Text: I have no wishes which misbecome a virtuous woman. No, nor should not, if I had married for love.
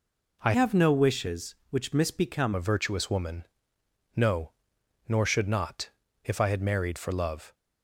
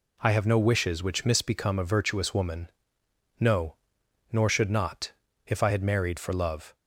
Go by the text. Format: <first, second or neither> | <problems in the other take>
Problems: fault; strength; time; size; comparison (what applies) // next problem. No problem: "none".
second | changes voice from "have" to "misbecome"; from 0.5 to 2.5 s; 2.0 s long